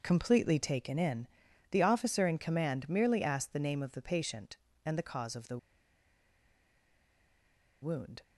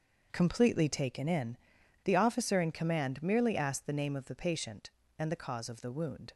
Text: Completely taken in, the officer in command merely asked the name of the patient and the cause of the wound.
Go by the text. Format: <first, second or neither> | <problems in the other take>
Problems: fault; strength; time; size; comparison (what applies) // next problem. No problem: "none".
second | starts louder than the rest; until 1.0 s; 6.5 dB; also in the second // pauses between "the" and "wound"; strong; at 5.5 s; 2.2 s long